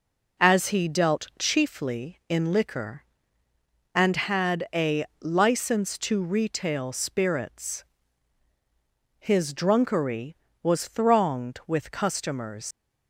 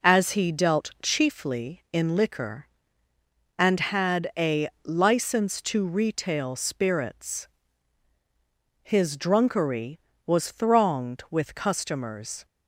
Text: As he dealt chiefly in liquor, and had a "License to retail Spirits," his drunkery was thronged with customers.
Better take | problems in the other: second | pauses between "a" and "License"; slight; at 5.0 s; 0.16 s long; slight in the second // leaves "customers" unfinished; at 12.7 s; 105 ms

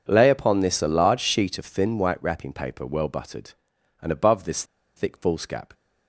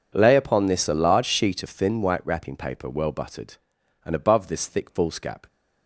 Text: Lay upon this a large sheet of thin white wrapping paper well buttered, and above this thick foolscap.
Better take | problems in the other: second | pauses between "this" and "thick"; slight; at 4.6 s; 0.33 s long

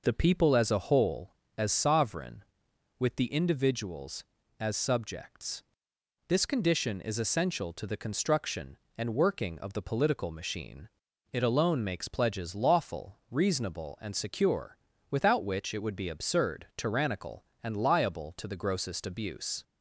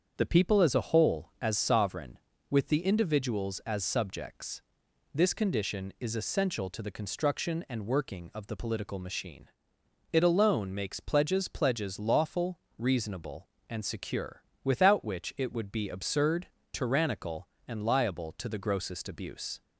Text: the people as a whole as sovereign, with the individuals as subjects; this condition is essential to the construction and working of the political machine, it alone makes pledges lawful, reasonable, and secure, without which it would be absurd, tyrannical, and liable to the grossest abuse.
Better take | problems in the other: first | starts louder than the rest; strong; until 1.1 s; 7 dB // says "pledges" twice; at 11.4 s

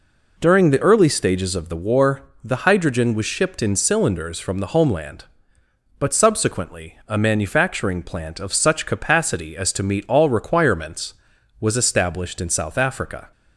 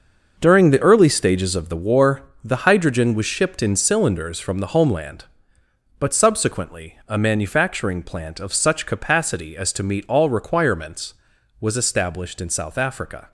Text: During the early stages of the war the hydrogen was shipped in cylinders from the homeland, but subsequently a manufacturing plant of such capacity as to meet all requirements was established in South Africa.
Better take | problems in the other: first | gets quieter; strong; throughout; 10.5 dB // pauses between "war" and "the"; slight; at 2.2 s; 0.22 s long; slight in the first

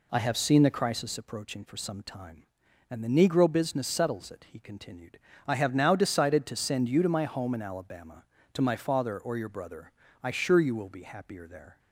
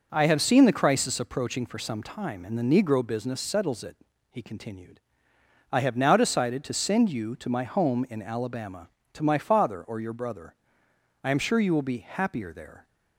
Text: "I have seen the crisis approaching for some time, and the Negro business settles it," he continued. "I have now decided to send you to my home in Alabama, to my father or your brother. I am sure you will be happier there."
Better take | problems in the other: second | skips "am"; at 10.3 s

